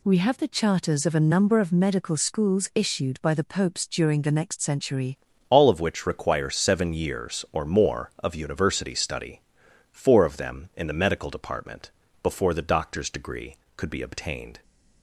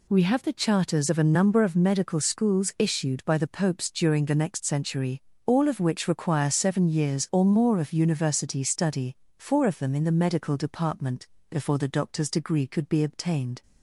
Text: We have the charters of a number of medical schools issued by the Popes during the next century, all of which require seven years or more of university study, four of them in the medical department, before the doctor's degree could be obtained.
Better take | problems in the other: second | changes voice at "all"; from 5.4 s on; 9.2 s long

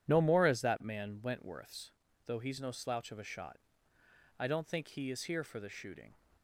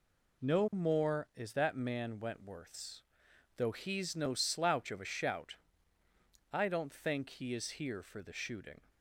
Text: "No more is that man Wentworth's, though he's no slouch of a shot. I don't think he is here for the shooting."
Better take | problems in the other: first | says "shout" for "shot"; at 5.0 s

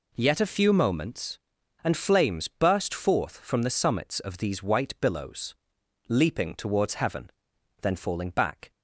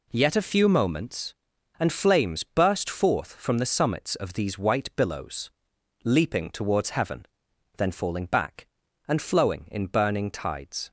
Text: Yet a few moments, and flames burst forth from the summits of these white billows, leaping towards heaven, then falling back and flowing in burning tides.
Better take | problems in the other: second | stops before "and flowing in burning tides"; at 8.7 s

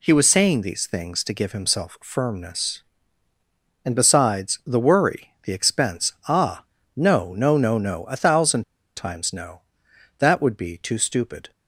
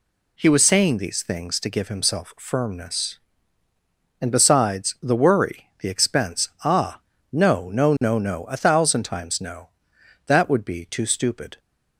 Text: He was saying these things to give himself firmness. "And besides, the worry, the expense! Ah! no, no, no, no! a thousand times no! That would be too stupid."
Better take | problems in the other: second | pauses between "thousand" and "times"; slight; at 8.6 s; 0.34 s long

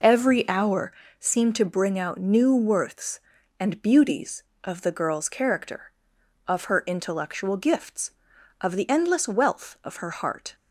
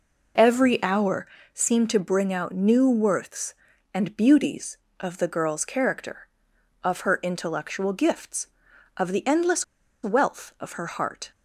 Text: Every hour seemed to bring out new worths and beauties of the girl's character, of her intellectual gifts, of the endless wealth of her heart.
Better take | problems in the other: first | pauses between "hour" and "seemed"; slight; at 1.2 s; 0.28 s long; slight in the first // pauses between "endless" and "wealth"; at 9.6 s; 0.38 s long

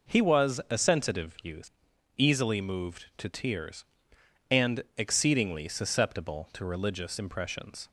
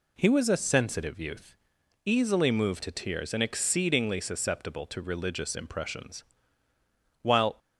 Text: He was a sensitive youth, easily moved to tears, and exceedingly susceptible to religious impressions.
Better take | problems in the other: first | goes on to say "While"; slight; from 7.2 s on; 0.36 s long

